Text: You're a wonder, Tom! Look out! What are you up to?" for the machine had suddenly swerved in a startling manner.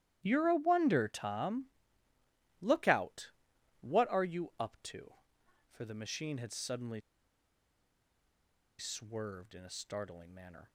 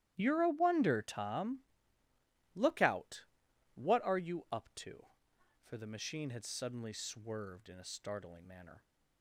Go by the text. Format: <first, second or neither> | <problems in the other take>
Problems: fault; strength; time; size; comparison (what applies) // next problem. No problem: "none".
second | starts louder than the rest; strong; until 1.2 s; 12.5 dB; strong in the second // pauses between "suddenly" and "swerved"; strong; at 7.0 s; 1.7 s long